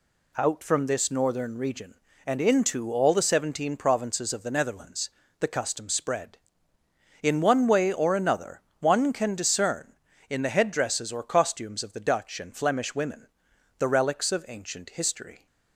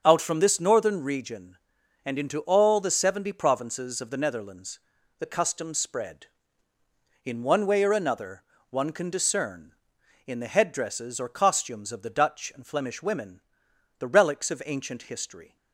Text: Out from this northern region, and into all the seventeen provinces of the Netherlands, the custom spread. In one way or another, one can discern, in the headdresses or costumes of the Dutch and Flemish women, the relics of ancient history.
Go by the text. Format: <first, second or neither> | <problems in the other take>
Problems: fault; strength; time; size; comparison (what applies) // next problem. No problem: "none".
first | starts louder than the rest; until 1.0 s; 6.5 dB // says "seventy" for "seventeen"; at 2.9 s